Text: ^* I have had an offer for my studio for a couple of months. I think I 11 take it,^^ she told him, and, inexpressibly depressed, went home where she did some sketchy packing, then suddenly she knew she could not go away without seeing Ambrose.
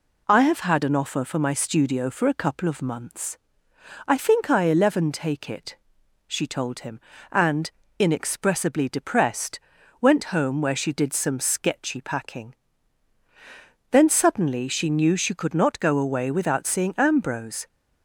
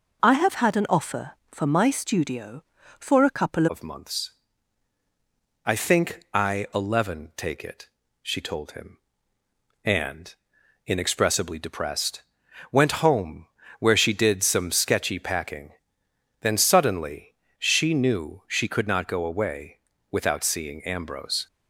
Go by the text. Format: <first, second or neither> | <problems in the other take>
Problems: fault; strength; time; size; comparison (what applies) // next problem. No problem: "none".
first | changes voice at "of"; from 3.6 s on; 17.8 s long // pauses between "home" and "where"; slight; at 13.4 s; 0.32 s long // pauses between "suddenly" and "she"; slight; at 17.3 s; 0.24 s long // pauses between "away" and "without"; slight; at 19.7 s; 0.32 s long